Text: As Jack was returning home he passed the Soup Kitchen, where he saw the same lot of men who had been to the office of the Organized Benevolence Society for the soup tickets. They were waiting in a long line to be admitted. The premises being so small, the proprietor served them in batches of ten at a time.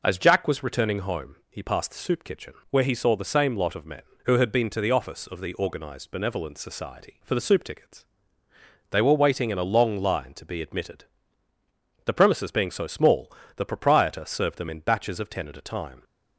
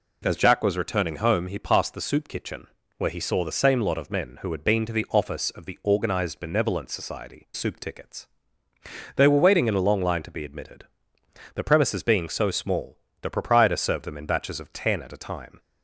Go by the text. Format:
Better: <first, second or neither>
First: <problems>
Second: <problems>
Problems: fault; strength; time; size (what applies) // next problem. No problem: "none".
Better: first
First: none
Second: skips "for the"; at 7.5 s